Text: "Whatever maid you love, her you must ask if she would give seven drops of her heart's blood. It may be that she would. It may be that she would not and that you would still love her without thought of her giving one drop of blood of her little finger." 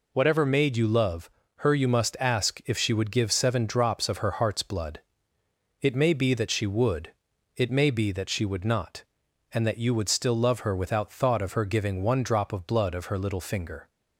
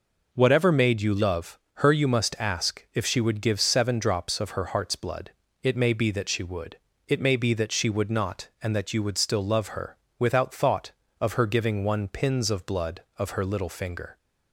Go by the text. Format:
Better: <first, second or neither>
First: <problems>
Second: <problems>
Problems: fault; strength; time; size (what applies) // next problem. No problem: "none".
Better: first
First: none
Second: pauses between "her" and "without"; slight; at 9.9 s; 0.20 s long // says "pins" for "drop"; at 12.0 s